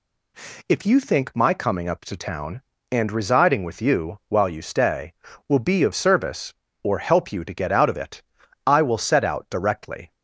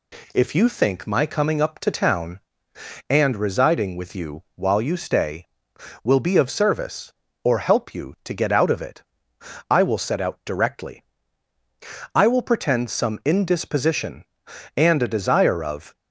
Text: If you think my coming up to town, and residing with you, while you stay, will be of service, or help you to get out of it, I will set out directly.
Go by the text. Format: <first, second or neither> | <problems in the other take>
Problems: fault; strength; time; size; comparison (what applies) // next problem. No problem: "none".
first | goes on to say "I will pretend some indisposition and a desire of"; strong; from 12.1 s on; 3.8 s long